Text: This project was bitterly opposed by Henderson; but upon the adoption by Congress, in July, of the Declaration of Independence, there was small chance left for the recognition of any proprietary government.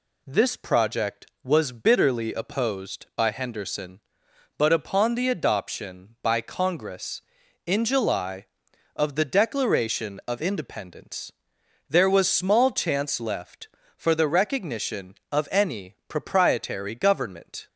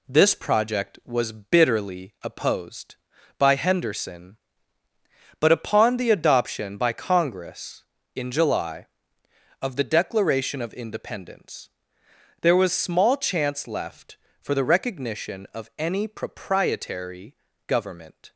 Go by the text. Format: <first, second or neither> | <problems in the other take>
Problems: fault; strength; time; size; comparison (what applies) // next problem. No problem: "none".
first | gets quieter; noticeable; throughout; 4 dB // pauses between "proprietary" and "government"; slight; at 17.3 s; 0.32 s long